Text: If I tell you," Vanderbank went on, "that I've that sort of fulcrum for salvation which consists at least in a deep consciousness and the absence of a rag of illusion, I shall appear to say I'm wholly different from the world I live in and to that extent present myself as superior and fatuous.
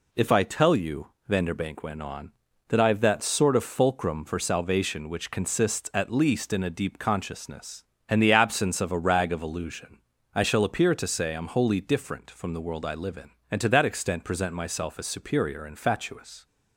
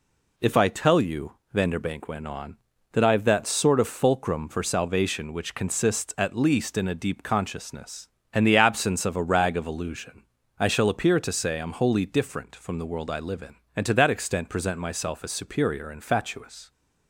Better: neither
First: none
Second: none

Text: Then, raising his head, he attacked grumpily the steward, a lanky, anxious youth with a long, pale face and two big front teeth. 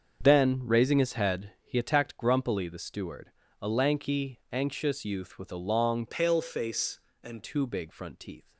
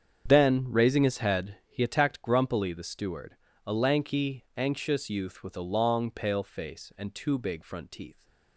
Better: second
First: starts louder than the rest; until 1.2 s; 7 dB // changes voice from "pale" to "and"; from 6.0 to 7.4 s; 1.4 s long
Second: starts louder than the rest; strong; until 1.3 s; 7.5 dB

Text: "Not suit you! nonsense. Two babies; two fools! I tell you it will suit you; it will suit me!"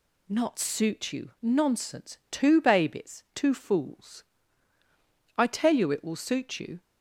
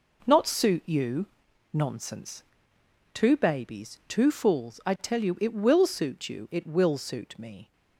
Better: second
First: stops before "it will suit me"; at 6.8 s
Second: none

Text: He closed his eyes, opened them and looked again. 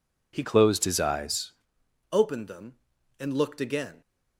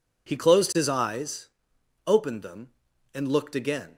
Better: second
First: changes voice from "closed" to "eyes"; from 0.4 to 1.5 s; 1.1 s long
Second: none

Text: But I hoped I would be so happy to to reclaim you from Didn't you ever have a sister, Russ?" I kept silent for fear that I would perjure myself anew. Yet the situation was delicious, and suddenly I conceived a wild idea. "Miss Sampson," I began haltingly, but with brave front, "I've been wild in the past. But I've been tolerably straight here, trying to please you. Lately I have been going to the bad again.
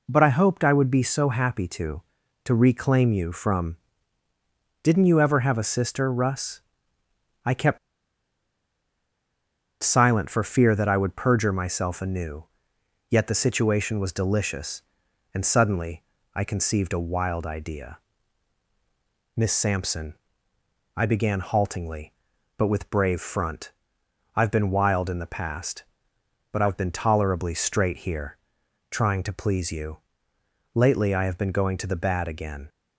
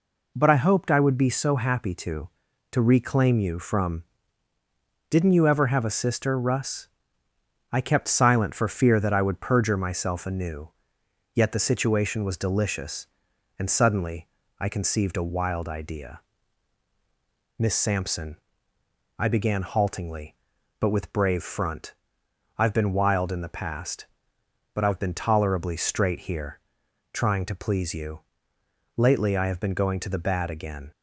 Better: second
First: pauses between "from" and "Didn't"; at 3.7 s; 1.0 s long // pauses between "kept" and "silent"; strong; at 7.7 s; 2.0 s long // pauses between "suddenly" and "I"; slight; at 16.0 s; 0.32 s long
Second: pauses between "from" and "Didn't"; at 4.0 s; 1.0 s long // pauses between "suddenly" and "I"; slight; at 14.2 s; 0.32 s long

